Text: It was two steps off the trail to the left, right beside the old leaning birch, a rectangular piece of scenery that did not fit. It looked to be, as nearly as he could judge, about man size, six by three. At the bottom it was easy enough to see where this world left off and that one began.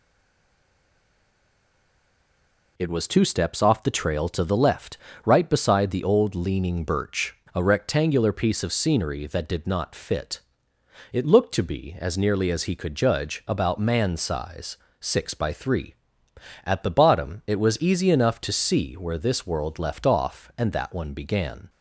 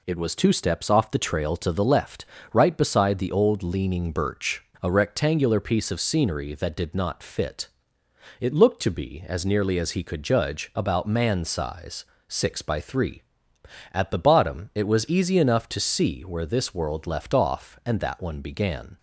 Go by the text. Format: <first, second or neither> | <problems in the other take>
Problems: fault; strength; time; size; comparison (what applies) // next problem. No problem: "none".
second | stays silent before the first word; strong; until 2.7 s; 2.7 s long